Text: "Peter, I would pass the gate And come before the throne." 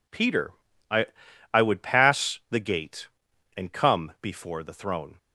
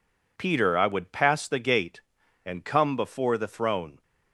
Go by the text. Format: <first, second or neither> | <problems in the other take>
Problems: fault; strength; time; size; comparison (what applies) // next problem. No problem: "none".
second | says "I" twice; at 1.5 s